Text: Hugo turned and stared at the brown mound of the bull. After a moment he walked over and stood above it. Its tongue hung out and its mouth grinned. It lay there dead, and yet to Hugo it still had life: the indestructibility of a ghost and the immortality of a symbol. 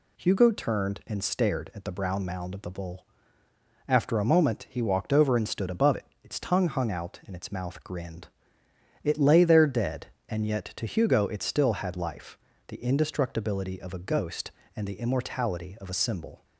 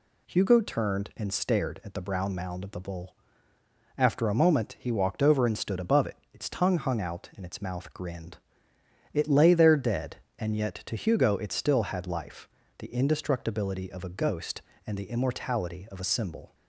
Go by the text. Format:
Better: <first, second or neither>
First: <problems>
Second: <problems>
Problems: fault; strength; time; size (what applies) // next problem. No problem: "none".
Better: neither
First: none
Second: none